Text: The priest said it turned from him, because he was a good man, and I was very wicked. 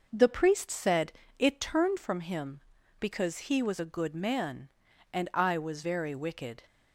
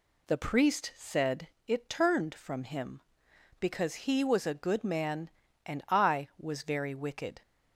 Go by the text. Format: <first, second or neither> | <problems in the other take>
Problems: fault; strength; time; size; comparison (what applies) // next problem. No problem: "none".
second | starts louder than the rest; noticeable; until 1.8 s; 5.5 dB // pauses between "said" and "it"; slight; at 1.1 s; 0.26 s long; slight in the second